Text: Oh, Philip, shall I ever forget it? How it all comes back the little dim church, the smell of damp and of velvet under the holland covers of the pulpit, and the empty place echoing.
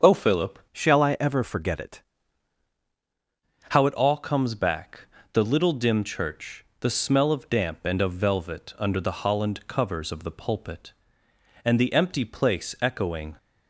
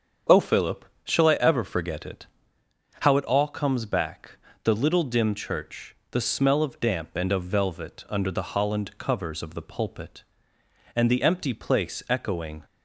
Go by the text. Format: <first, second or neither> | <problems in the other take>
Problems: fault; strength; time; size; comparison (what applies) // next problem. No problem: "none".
second | starts louder than the rest; until 1.2 s; 7 dB; strong in the second // changes voice from "shall" to "it"; from 0.7 to 2.0 s; 1.3 s long // pauses between "back" and "the"; slight; at 5.0 s; 0.32 s long; slight in the second